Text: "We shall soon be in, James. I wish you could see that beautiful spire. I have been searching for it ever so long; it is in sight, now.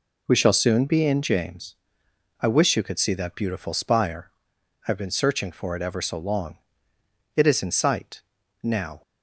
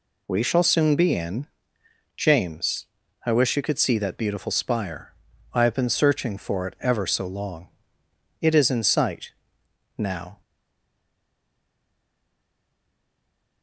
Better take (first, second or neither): first